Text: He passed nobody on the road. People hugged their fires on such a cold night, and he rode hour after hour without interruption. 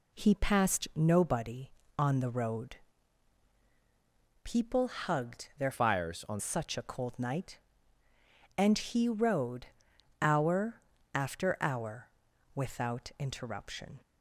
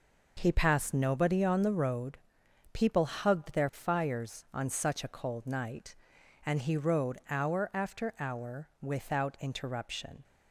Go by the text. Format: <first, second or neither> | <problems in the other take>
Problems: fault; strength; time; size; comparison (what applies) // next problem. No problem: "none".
second | changes voice from "fires" to "on"; from 5.7 to 6.4 s; 0.7 s long // pauses between "rode" and "hour"; noticeable; at 9.6 s; 0.56 s long // pauses between "hour" and "after"; slight; at 10.8 s; 0.34 s long // pauses between "hour" and "without"; noticeable; at 12.0 s; 0.46 s long